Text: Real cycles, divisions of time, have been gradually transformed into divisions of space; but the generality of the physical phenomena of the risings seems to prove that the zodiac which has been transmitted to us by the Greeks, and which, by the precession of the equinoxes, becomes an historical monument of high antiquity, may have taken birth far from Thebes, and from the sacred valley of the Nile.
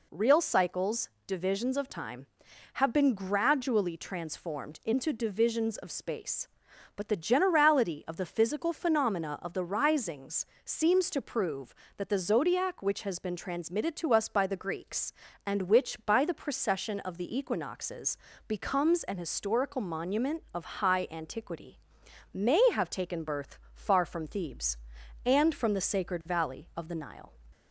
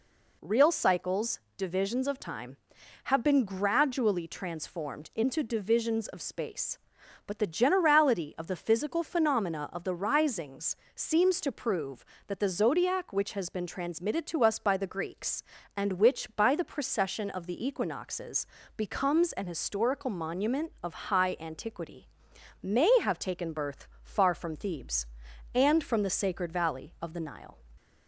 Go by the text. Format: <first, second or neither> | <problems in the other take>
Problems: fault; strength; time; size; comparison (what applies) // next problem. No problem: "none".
neither | pauses between "risings" and "seems"; slight; the same in both // pauses between "birth" and "far"; slight; the same in both